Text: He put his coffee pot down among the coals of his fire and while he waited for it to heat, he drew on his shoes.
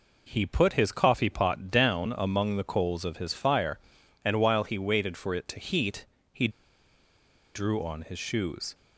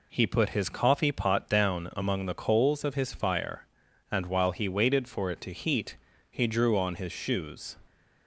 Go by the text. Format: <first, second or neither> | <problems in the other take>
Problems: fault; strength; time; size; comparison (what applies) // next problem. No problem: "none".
second | pauses between "he" and "drew"; at 6.4 s; 1.0 s long